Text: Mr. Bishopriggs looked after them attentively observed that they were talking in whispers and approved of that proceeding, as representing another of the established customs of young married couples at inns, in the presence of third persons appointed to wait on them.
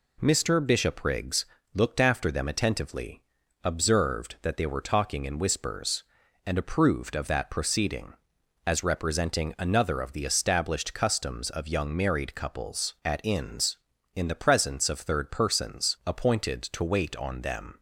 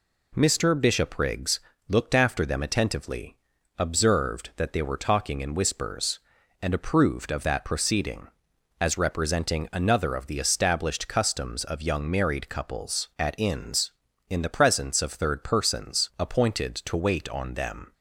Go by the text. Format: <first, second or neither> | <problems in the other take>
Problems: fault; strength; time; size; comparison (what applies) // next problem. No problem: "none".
neither | pauses between "Bishopriggs" and "looked"; slight; the same in both // pauses between "attentively" and "observed"; the same in both